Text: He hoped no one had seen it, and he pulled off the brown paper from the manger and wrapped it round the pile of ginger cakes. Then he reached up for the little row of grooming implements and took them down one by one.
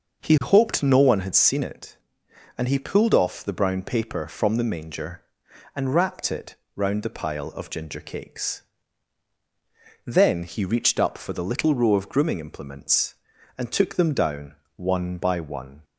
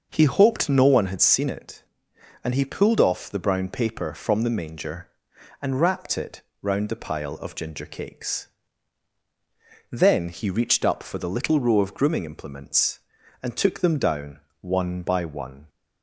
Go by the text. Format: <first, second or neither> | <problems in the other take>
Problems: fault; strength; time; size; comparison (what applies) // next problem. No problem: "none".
neither | pauses between "it" and "round"; slight; the same in both // pauses between "down" and "one"; slight; the same in both